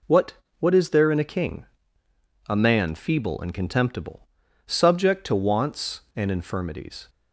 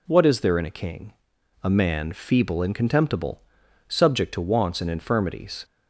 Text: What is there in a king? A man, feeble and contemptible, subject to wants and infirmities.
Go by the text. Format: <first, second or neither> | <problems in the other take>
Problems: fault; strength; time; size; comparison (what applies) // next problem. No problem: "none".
second | says "What" twice; at 0.5 s